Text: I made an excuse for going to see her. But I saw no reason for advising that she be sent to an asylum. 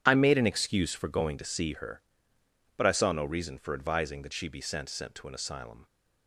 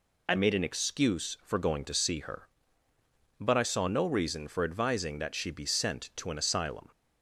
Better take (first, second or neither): second